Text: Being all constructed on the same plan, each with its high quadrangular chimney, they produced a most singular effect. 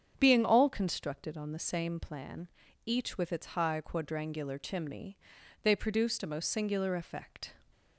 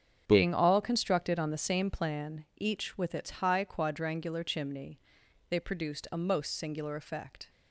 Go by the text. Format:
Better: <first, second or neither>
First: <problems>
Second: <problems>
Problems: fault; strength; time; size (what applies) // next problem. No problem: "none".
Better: neither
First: starts louder than the rest; strong; until 1.1 s; 7.5 dB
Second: starts louder than the rest; strong; until 1.2 s; 7.5 dB